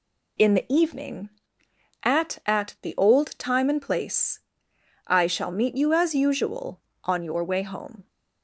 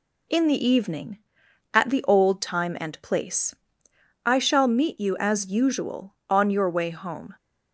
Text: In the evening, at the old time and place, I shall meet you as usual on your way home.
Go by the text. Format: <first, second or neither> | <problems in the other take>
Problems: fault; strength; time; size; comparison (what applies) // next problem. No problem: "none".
second | says "at" twice; at 2.4 s